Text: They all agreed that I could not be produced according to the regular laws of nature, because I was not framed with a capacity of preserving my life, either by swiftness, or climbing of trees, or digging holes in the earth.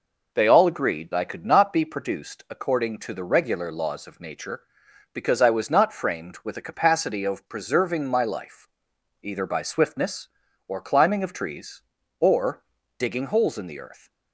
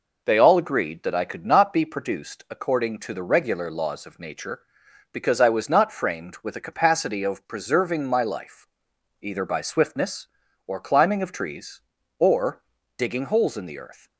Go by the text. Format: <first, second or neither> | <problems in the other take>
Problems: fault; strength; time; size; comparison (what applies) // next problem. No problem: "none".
second | skips "that"; at 1.1 s // pauses between "or" and "digging"; slight; at 12.6 s; 0.36 s long; slight in the second